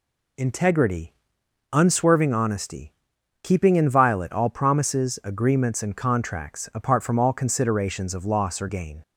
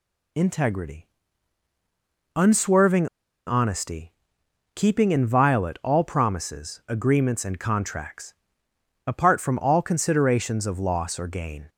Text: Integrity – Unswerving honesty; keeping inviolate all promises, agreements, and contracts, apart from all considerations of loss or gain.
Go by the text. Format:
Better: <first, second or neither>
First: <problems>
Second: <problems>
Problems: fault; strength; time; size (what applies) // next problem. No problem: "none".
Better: first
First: none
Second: pauses between "Unswerving" and "honesty"; at 3.0 s; 0.40 s long